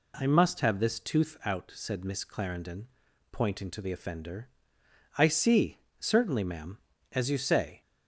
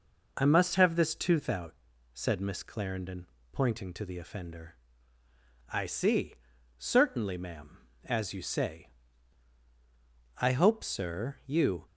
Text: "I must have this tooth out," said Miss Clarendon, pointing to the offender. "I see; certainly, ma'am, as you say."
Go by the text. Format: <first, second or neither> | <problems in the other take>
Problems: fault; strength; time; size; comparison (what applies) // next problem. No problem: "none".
first | goes on to say "I hope sir you"; from 10.4 s on; 1.4 s long